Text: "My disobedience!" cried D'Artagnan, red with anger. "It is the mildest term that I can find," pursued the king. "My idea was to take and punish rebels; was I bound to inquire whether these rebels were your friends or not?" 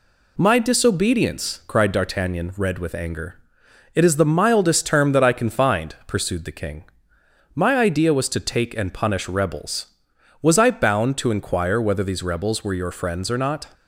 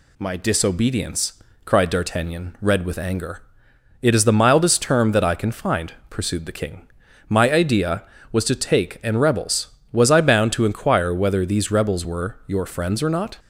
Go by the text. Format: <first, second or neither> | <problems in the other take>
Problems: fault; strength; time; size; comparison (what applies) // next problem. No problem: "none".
first | skips "punish"; at 9.1 s